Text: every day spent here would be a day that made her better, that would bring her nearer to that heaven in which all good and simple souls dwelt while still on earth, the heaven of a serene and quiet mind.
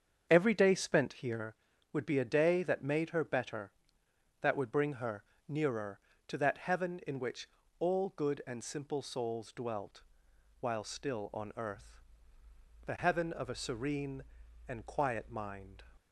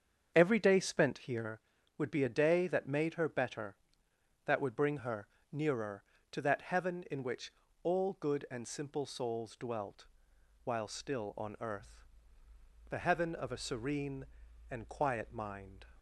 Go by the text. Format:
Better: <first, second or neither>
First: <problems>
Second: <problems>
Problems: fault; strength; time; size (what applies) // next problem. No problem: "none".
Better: neither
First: starts louder than the rest; strong; until 1.2 s; 7 dB // pauses between "her" and "nearer"; slight; at 5.2 s; 0.24 s long // pauses between "which" and "all"; slight; at 7.4 s; 0.32 s long // pauses between "dwelt" and "while"; noticeable; at 10.0 s; 0.58 s long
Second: starts louder than the rest; strong; until 1.3 s; 7 dB // pauses between "her" and "nearer"; slight; at 5.2 s; 0.24 s long // pauses between "which" and "all"; slight; at 7.5 s; 0.32 s long // pauses between "dwelt" and "while"; noticeable; at 10.0 s; 0.58 s long